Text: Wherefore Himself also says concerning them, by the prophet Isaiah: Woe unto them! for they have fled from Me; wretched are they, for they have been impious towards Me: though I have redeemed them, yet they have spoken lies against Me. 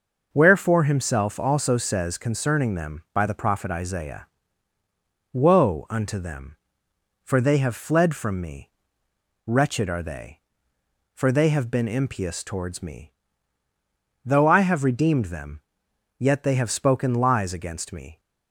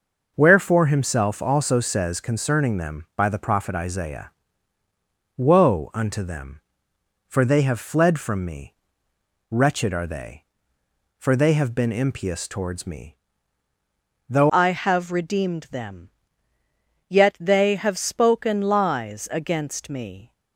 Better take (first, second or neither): first